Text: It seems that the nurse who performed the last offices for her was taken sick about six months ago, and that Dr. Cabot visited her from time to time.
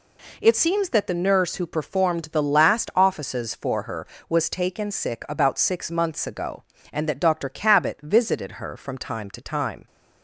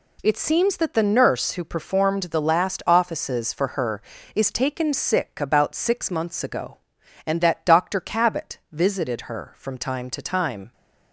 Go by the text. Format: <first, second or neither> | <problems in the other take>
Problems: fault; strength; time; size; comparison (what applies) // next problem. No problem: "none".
first | says "is" for "was"; at 4.3 s